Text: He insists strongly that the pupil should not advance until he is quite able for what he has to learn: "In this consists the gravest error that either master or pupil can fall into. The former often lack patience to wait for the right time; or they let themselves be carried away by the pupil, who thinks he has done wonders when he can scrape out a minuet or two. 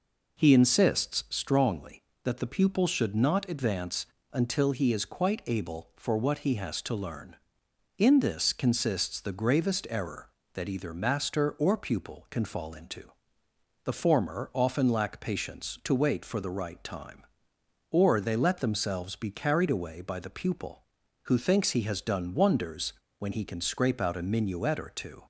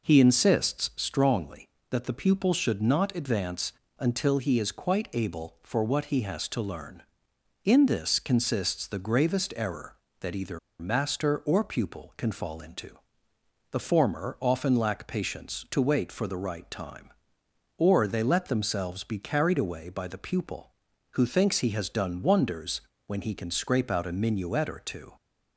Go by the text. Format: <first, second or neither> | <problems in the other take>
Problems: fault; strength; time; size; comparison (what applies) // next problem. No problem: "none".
first | pauses between "advance" and "until"; slight; at 3.7 s; 0.26 s long; slight in the first // pauses between "either" and "master"; slight; at 10.5 s; 0.21 s long // pauses between "wonders" and "when"; slight; at 22.8 s; 0.24 s long; slight in the first